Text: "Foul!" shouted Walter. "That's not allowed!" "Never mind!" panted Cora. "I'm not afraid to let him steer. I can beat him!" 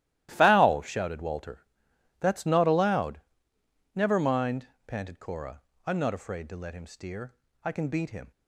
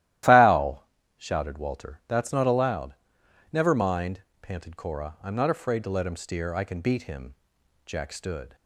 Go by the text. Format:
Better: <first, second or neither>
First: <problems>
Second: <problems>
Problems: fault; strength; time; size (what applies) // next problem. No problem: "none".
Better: first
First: starts louder than the rest; strong; until 1.3 s; 14.5 dB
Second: starts louder than the rest; strong; until 1.5 s; 14 dB // goes on to say "Jack stood"; noticeable; from 7.8 s on; 0.70 s long